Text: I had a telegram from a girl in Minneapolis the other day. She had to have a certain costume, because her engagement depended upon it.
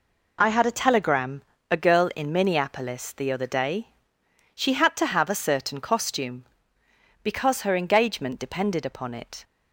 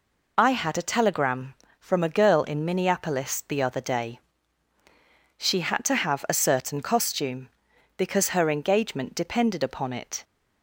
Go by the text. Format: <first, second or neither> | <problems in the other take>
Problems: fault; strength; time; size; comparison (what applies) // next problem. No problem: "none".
second | skips "from"; at 1.5 s